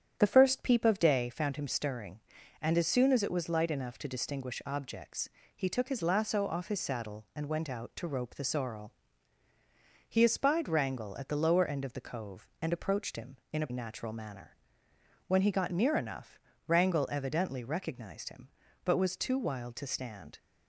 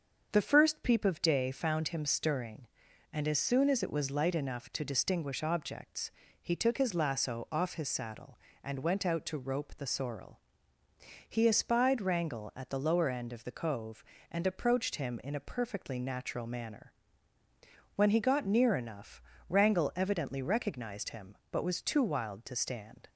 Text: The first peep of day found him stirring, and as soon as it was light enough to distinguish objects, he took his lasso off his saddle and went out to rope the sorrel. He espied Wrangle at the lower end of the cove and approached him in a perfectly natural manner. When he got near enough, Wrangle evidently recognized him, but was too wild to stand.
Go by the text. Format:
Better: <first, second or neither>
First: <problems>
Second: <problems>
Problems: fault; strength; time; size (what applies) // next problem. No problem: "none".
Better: second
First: starts louder than the rest; strong; until 1.2 s; 9 dB // skips "perfectly"; at 13.7 s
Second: starts louder than the rest; until 1.3 s; 6.5 dB